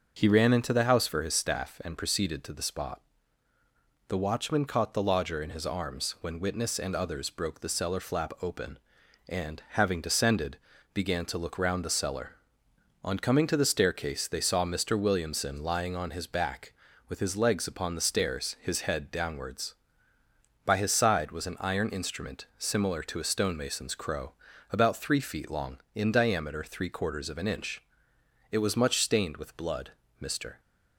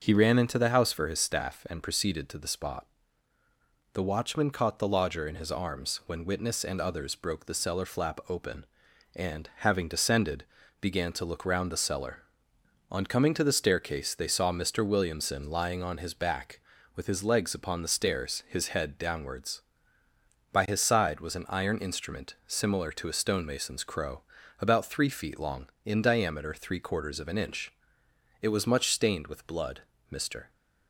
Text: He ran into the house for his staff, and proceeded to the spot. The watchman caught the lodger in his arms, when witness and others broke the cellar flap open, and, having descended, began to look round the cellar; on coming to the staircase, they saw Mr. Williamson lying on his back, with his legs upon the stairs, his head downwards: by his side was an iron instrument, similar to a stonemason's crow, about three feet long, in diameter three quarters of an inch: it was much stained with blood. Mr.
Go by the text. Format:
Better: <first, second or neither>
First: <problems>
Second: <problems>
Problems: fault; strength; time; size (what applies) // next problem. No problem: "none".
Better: neither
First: starts louder than the rest; noticeable; until 1.1 s; 6 dB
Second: starts louder than the rest; noticeable; until 1.0 s; 6 dB